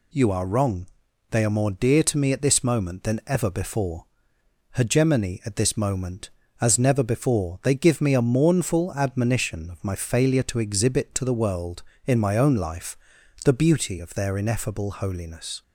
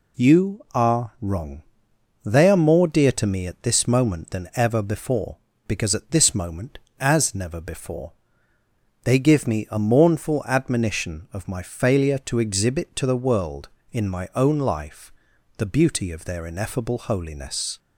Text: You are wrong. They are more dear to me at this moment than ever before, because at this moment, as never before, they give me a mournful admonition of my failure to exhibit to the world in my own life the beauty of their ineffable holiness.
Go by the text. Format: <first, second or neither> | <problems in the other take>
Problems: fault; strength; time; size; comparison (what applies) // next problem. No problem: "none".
second | says "hegemony" for "because"; at 4.7 s // pauses between "life" and "the"; noticeable; at 12.9 s; 0.50 s long; noticeable in the second